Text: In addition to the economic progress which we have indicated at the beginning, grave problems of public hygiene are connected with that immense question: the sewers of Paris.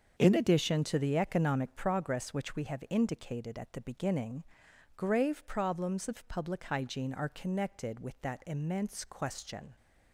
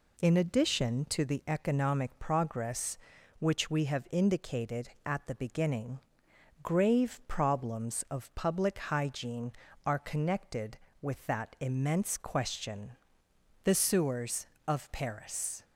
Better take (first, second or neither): second